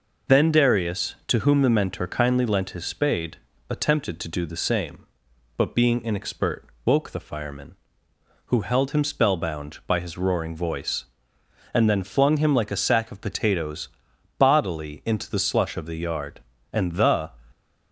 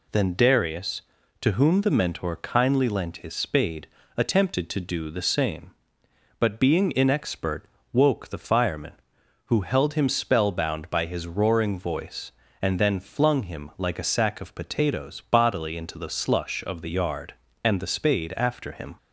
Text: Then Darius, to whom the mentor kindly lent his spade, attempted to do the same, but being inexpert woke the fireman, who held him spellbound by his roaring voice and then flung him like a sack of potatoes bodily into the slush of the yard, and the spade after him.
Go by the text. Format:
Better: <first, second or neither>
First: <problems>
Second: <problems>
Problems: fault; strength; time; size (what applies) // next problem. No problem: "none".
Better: second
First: pauses between "inexpert" and "woke"; slight; at 6.6 s; 0.22 s long // pauses between "potatoes" and "bodily"; noticeable; at 13.8 s; 0.48 s long // stops before "spade after him"; at 17.5 s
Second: pauses between "inexpert" and "woke"; slight; at 7.6 s; 0.28 s long